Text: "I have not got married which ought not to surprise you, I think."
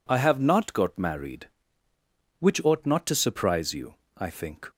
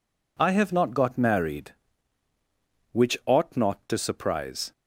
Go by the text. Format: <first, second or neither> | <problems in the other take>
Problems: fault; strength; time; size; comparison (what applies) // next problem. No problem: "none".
first | stops before "you I think"; at 4.7 s